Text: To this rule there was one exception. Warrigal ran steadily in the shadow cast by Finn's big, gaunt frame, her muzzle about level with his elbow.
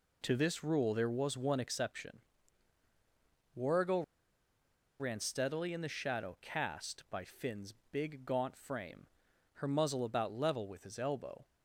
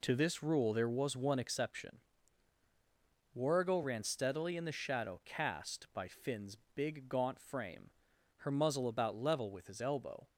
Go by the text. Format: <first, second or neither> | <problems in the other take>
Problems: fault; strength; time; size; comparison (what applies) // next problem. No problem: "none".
second | pauses between "Warrigal" and "ran"; noticeable; at 4.0 s; 0.96 s long // pauses between "Finn's" and "big"; slight; at 7.7 s; 0.18 s long; slight in the second